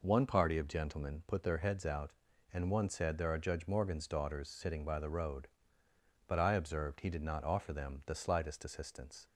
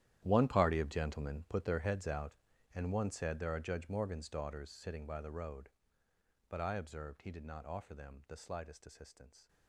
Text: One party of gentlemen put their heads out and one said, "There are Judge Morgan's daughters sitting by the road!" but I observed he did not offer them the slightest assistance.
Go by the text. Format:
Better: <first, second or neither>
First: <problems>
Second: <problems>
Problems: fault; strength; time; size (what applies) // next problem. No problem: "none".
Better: first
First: none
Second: gets quieter; strong; throughout; 17 dB